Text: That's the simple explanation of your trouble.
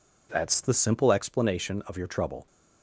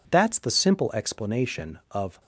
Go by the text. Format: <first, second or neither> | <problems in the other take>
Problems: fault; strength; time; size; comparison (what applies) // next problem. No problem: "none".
first | stops before "your trouble"; at 2.1 s